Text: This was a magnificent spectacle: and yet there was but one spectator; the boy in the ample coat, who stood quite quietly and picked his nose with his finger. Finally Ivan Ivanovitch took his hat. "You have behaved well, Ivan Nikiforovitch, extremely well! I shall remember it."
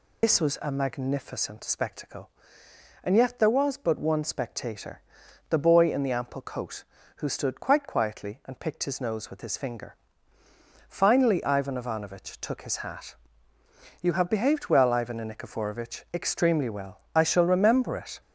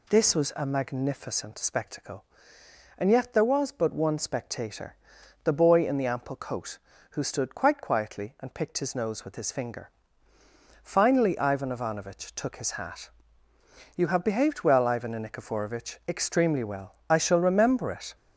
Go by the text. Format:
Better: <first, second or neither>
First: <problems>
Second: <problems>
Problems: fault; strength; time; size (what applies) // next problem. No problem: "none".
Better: second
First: loses the start of "This"; at 0.2 s; 90 ms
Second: none